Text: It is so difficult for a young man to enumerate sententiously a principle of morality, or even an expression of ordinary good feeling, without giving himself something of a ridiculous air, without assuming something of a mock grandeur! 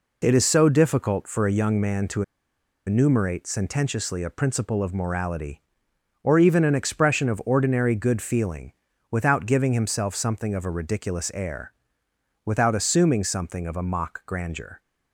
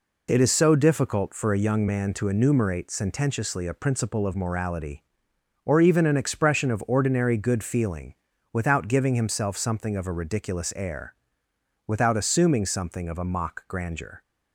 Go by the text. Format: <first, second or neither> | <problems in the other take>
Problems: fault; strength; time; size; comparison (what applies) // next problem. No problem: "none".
second | pauses between "to" and "enumerate"; noticeable; at 2.2 s; 0.63 s long